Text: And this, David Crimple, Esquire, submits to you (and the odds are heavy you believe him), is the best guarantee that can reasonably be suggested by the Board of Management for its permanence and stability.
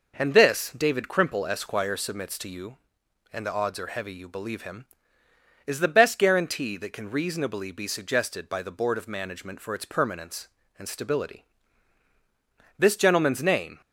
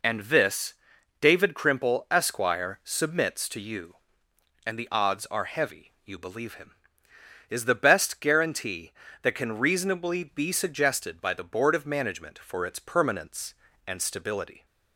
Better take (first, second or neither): second